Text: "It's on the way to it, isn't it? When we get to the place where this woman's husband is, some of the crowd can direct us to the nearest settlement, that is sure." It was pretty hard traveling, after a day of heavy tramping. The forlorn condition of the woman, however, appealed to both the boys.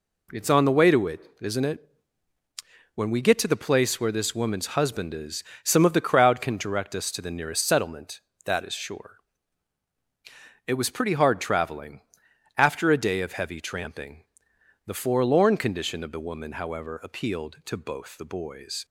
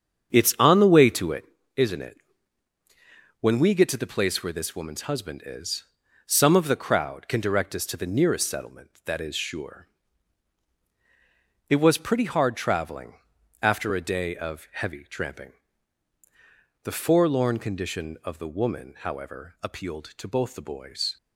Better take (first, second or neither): first